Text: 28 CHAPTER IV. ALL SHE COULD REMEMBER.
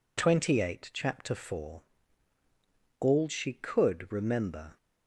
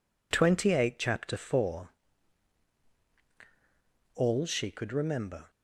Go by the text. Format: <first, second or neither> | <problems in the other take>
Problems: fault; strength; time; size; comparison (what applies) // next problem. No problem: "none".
neither | none